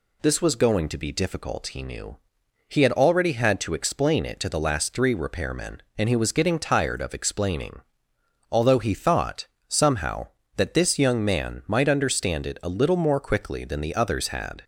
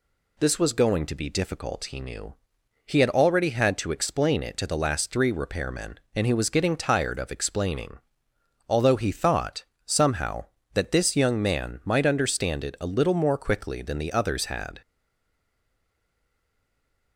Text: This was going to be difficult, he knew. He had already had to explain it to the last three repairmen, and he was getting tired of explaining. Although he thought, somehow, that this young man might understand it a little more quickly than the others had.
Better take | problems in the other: first | stays silent after the last word; from 14.8 s on; 2.3 s long

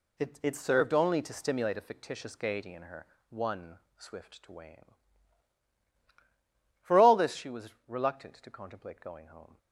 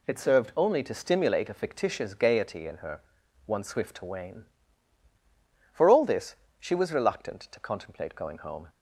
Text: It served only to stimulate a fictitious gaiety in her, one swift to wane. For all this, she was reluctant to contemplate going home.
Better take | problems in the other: second | says "It" twice; at 0.4 s // pauses between "one" and "swift"; slight; at 3.7 s; 0.18 s long

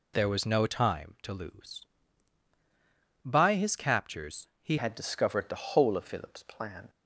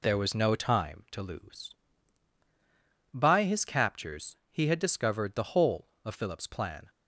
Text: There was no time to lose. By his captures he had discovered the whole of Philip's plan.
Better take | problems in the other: second | pauses between "captures" and "he"; slight; at 4.4 s; 0.16 s long; slight in the second // changes voice at "had"; from 4.7 s on; 2.1 s long

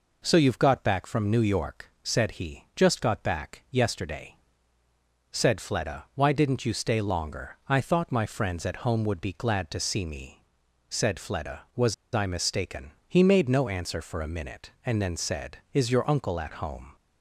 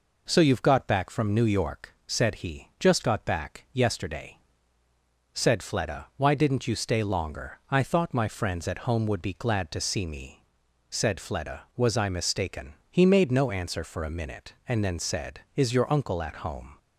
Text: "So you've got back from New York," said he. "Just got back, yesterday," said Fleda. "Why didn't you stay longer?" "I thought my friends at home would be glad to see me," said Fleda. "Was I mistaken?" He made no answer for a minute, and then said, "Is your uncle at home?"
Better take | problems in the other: second | pauses between "Was" and "I"; slight; at 11.9 s; 0.20 s long

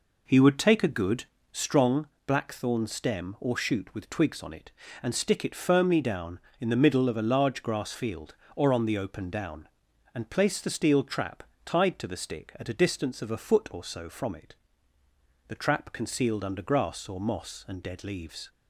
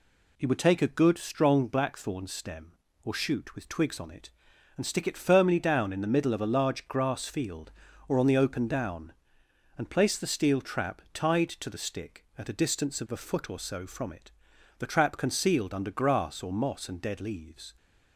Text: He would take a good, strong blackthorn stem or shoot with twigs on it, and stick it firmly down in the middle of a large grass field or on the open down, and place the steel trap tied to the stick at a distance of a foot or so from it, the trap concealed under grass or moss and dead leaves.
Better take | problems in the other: second | starts louder than the rest; noticeable; until 2.0 s; 4 dB // pauses between "strong" and "blackthorn"; slight; at 2.0 s; 0.18 s long // pauses between "trap" and "tied"; slight; at 11.4 s; 0.24 s long

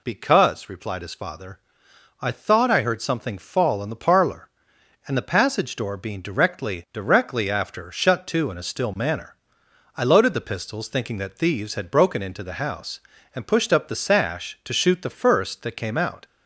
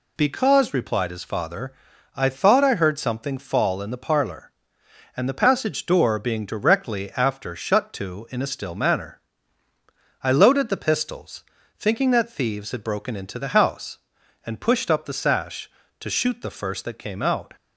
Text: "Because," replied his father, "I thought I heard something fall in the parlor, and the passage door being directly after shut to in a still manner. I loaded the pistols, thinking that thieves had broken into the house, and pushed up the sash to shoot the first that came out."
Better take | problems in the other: second | says "directly" twice; at 6.9 s

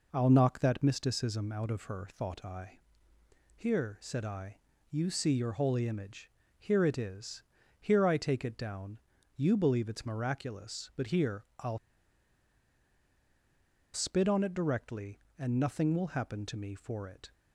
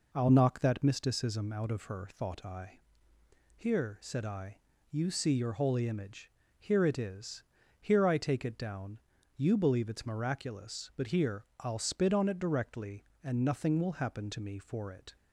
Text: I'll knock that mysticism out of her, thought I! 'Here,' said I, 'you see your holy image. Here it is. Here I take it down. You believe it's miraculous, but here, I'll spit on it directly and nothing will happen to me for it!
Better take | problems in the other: second | pauses between "I'll" and "spit"; strong; at 11.7 s; 2.1 s long

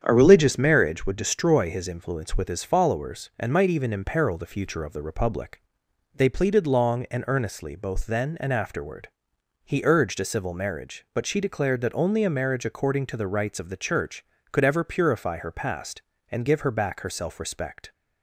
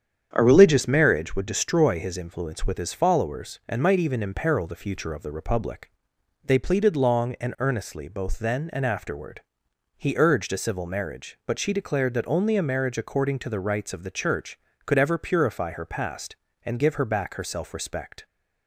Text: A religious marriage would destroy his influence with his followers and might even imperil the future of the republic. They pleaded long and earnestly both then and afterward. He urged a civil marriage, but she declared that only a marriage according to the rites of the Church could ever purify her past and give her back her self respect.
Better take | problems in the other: neither | starts louder than the rest; strong; the same in both

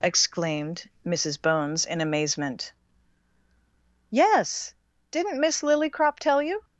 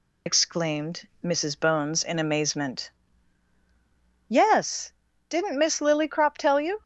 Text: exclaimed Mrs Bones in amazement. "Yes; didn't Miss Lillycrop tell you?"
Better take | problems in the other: first | loses the start of "exclaimed"; at 0.2 s; 70 ms

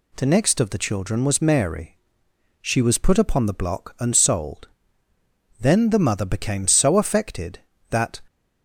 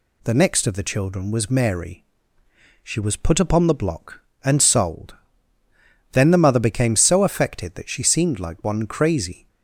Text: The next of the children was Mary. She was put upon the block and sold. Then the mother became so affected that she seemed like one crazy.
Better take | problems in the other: second | stops before "she seemed like one crazy"; at 8.2 s

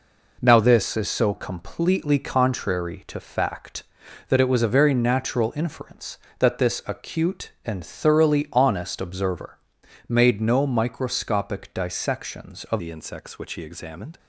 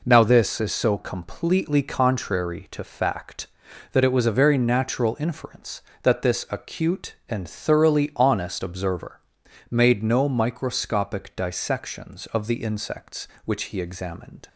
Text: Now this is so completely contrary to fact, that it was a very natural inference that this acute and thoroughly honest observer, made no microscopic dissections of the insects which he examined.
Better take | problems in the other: second | changes voice at "the"; from 12.7 s on; 1.4 s long

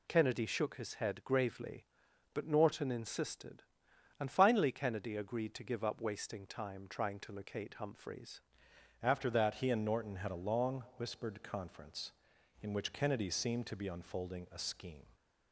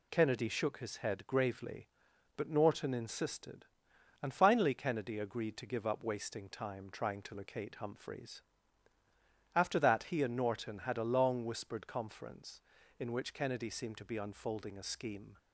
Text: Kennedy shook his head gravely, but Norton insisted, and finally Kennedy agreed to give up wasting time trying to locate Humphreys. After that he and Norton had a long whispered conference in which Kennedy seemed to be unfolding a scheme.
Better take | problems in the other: second | changes voice at "After"; from 9.0 s on; 6.0 s long

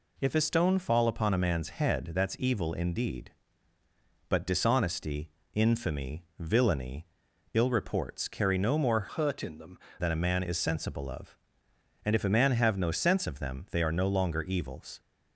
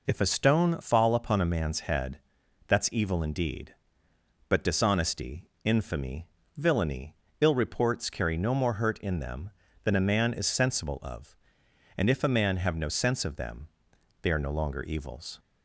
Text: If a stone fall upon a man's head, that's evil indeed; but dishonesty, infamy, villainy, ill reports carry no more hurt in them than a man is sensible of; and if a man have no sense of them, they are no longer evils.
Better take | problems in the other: second | changes voice from "hurt" to "them"; from 9.0 to 9.7 s; 0.7 s long

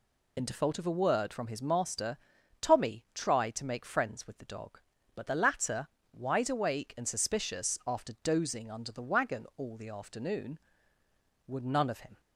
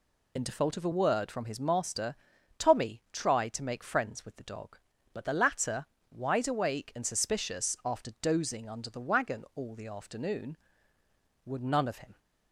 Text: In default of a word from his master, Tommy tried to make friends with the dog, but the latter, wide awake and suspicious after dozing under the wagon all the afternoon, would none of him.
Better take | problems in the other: neither | none

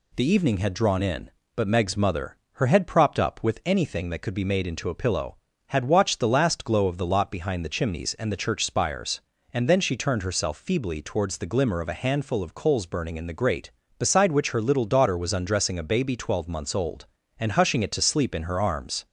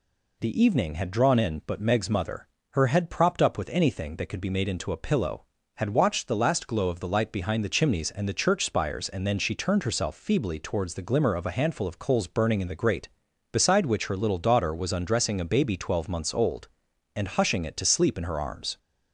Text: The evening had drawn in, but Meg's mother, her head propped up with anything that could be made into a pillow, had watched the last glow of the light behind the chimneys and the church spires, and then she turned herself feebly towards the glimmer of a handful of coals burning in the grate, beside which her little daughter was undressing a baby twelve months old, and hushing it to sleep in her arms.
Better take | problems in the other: second | says "lot" for "light"; at 7.0 s

